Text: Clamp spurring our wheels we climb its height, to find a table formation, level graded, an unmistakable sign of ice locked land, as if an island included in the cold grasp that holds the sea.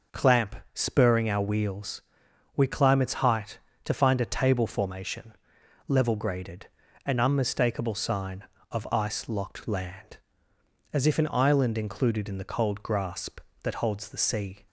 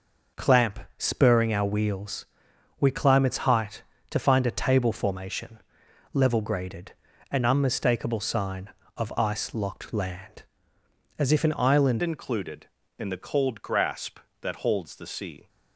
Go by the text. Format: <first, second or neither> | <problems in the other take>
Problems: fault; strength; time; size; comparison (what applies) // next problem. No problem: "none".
first | pauses between "Clamp" and "spurring"; slight; at 0.7 s; 0.18 s long; slight in the first // pauses between "wheels" and "we"; noticeable; at 2.2 s; 0.54 s long; noticeable in the first // changes voice at "included"; from 12.0 s on; 3.4 s long